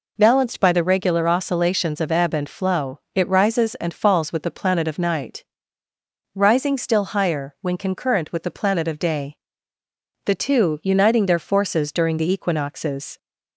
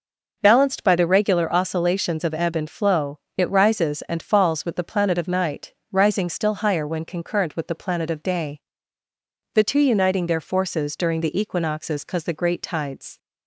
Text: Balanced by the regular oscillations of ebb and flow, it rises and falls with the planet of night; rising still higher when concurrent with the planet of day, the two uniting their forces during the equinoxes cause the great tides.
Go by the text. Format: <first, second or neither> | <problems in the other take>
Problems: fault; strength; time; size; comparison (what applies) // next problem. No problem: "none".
second | stops before "cause the great tides"; at 13.1 s